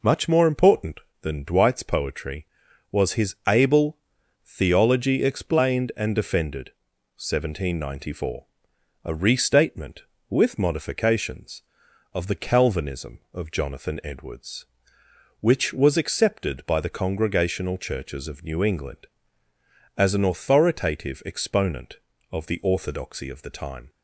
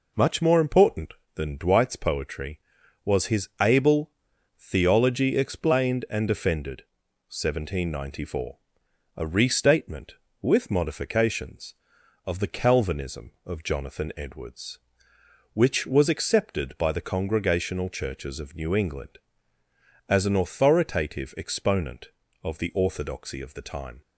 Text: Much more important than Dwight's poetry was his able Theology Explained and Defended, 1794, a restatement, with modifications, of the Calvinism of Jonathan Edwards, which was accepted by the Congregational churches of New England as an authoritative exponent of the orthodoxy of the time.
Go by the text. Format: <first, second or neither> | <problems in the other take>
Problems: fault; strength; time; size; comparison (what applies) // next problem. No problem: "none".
neither | pauses between "able" and "Theology"; noticeable; the same in both